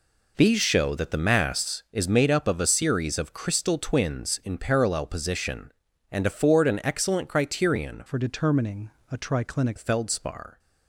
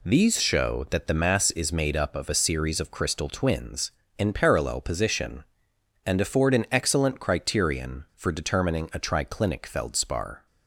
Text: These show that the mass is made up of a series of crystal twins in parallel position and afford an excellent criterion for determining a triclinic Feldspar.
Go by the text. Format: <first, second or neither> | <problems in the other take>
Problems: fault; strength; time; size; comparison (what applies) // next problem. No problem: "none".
second | changes voice from "for" to "triclinic"; from 8.0 to 9.7 s; 1.7 s long // pauses between "determining" and "a"; slight; at 8.9 s; 0.20 s long